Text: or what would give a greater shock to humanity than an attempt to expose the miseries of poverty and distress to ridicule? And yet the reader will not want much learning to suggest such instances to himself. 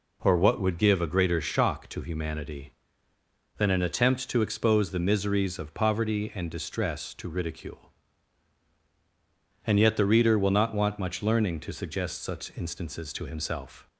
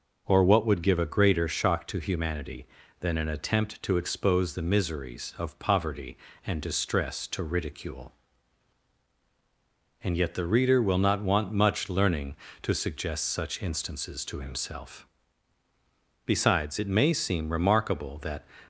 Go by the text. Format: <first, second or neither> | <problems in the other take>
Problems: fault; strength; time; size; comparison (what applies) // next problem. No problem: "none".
first | goes on to say "Besides it may seem remarkable that"; strong; from 16.2 s on; 2.1 s long